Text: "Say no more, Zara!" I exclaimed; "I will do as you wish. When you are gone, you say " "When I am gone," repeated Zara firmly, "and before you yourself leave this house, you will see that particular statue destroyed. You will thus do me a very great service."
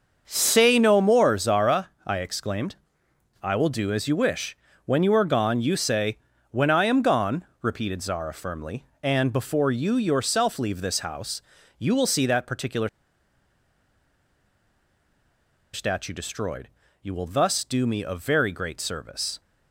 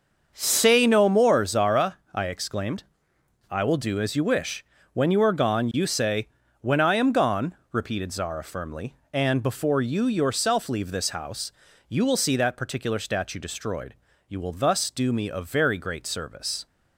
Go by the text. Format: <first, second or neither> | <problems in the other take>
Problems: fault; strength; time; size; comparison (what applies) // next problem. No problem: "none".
second | starts louder than the rest; until 1.2 s; 6.5 dB; also in the second // pauses between "particular" and "statue"; strong; at 12.8 s; 2.8 s long